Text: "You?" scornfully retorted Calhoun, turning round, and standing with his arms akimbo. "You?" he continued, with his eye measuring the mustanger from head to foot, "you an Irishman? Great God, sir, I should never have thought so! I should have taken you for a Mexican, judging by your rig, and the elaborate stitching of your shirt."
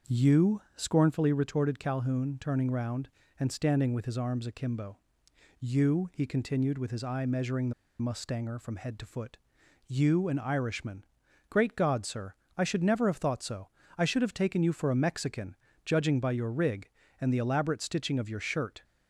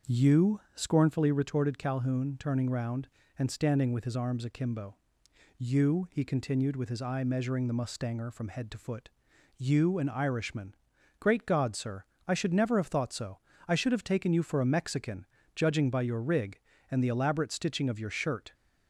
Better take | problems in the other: second | starts louder than the rest; until 1.2 s; 7 dB; also in the second // pauses between "the" and "mustanger"; slight; at 7.7 s; 0.28 s long

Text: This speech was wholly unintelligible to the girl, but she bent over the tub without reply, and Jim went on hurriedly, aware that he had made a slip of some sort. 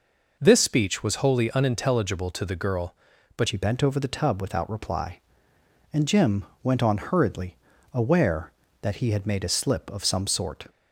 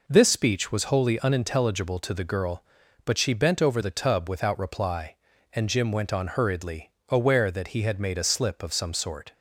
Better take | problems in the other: second | changes voice at "she"; from 3.4 s on; 7.2 s long // pauses between "Jim" and "went"; slight; at 6.4 s; 0.20 s long

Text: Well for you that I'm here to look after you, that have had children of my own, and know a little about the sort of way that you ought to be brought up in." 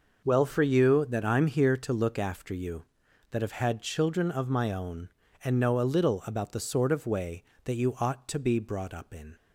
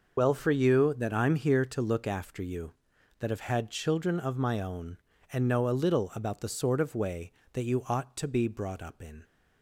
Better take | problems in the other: first | loses the start of "Well"; at 0.1 s; 40 ms

